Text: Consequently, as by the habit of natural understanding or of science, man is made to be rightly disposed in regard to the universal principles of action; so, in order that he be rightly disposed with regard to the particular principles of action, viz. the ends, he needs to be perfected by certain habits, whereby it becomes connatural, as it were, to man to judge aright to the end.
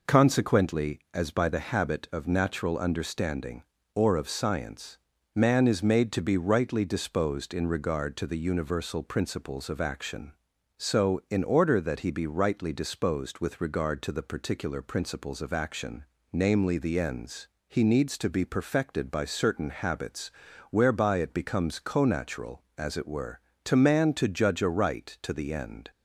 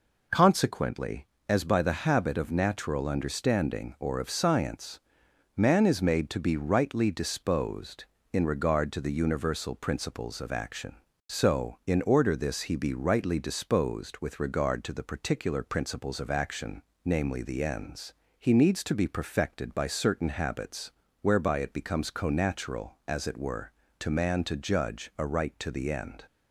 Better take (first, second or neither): first